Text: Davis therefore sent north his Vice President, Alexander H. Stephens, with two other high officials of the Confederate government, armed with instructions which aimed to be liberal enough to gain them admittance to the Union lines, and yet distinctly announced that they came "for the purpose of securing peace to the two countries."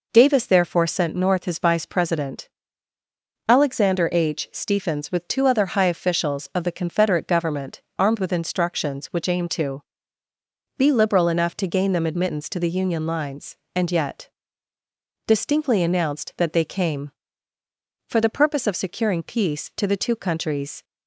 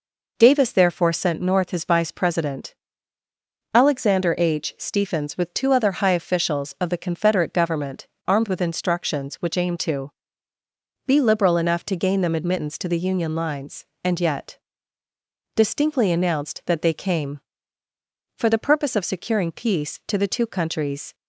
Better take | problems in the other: neither | pauses between "to" and "be"; noticeable; the same in both // pauses between "yet" and "distinctly"; noticeable; the same in both

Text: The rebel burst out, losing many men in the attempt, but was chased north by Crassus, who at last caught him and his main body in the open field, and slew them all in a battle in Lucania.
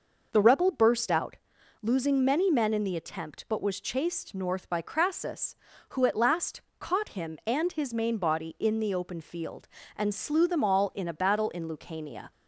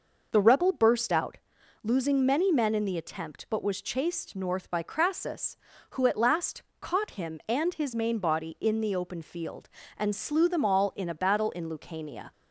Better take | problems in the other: neither | pauses between "last" and "caught"; slight; the same in both

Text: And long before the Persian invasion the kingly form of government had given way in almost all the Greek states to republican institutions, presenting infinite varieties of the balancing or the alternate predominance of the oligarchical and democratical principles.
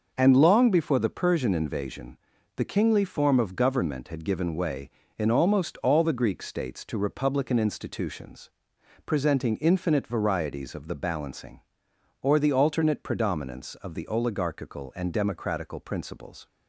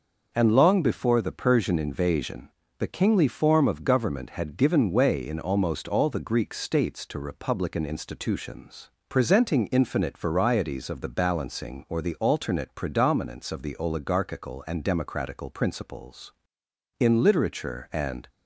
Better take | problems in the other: first | pauses between "invasion" and "the"; slight; at 2.5 s; 0.28 s long; also in the first // goes on to say "In literature and"; noticeable; from 16.9 s on; 1.3 s long

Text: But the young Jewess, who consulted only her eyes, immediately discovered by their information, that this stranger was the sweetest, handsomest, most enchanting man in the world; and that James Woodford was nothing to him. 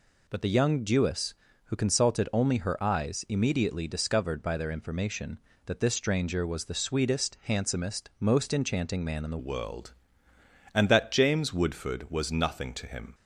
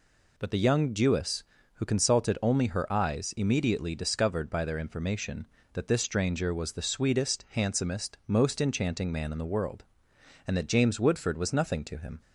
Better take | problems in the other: second | changes voice at "world"; from 9.3 s on; 3.8 s long

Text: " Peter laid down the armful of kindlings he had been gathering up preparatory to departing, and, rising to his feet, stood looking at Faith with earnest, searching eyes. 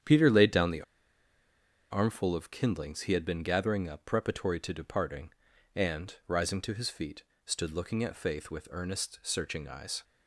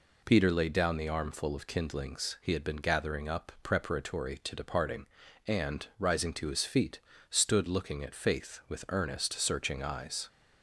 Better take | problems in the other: second | starts louder than the rest; strong; until 2.1 s; 9 dB // pauses between "the" and "armful"; at 0.8 s; 1.0 s long

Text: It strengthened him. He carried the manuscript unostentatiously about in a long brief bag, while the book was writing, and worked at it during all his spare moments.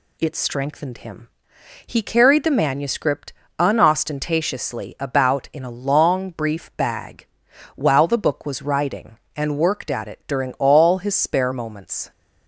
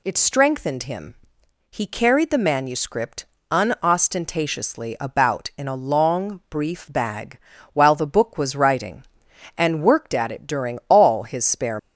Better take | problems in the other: first | pauses between "manuscript" and "unostentatiously"; slight; at 3.2 s; 0.26 s long; slight in the first // stops before "moments"; at 11.7 s

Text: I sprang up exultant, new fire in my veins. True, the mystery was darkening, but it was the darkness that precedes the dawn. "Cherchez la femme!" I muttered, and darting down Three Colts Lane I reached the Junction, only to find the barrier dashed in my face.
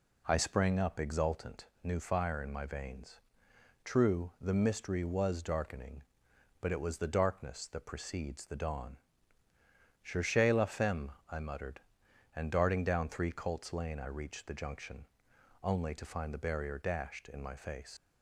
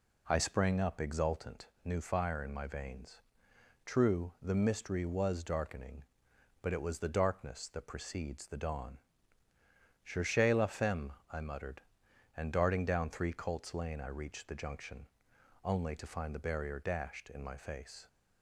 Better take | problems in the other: second | leaves "face" unfinished; at 17.9 s; 95 ms

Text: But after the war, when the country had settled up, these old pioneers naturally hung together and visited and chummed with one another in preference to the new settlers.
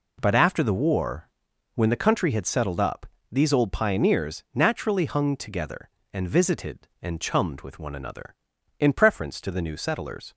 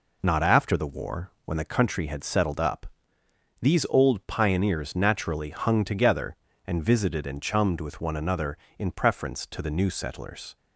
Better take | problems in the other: first | says "Not" for "But"; at 0.2 s

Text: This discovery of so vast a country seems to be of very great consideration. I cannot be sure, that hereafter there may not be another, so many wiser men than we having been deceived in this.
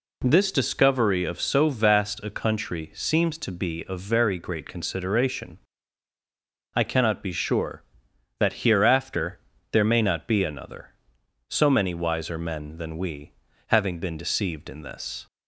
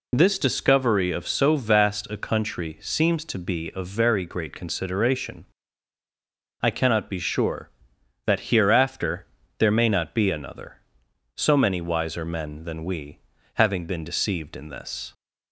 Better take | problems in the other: first | loses the start of "This"; at 0.1 s; 50 ms // pauses between "hereafter" and "there"; slight; at 9.2 s; 0.34 s long; slight in the first // pauses between "we" and "having"; slight; at 13.1 s; 0.34 s long; slight in the first

